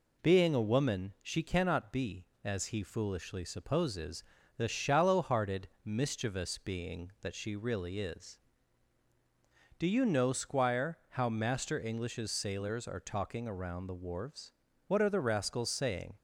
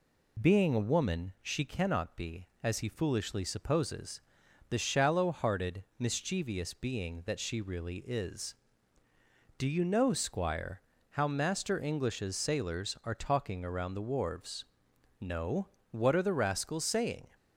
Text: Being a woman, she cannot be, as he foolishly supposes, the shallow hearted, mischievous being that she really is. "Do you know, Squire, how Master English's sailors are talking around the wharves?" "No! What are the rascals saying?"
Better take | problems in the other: second | skips "No"; at 14.6 s

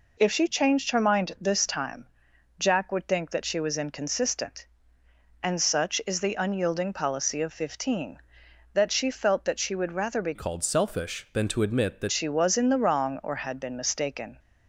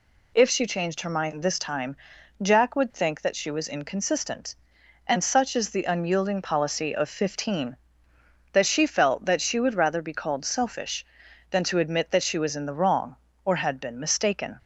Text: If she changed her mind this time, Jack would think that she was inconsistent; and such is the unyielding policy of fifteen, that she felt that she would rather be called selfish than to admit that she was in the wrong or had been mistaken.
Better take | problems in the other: second | changes voice from "called" to "that"; from 10.3 to 12.1 s; 1.8 s long

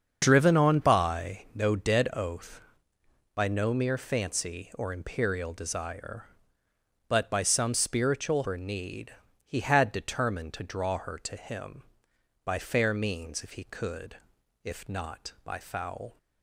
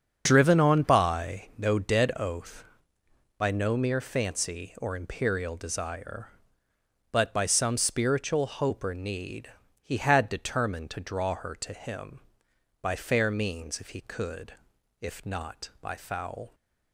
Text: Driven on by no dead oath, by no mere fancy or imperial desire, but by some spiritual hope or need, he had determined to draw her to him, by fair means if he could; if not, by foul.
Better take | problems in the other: second | starts louder than the rest; until 1.2 s; 7 dB; also in the second // skips "hope"; at 8.4 s

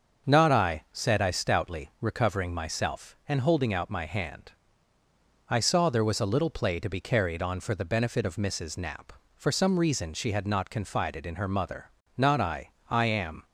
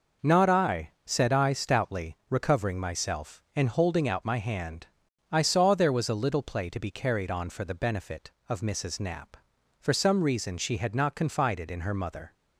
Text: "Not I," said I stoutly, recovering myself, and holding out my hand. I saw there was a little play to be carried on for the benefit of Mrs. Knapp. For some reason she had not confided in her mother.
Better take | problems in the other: second | starts louder than the rest; until 1.3 s; 6.5 dB // goes on to say "Not I I am"; noticeable; from 12.1 s on; 1.2 s long

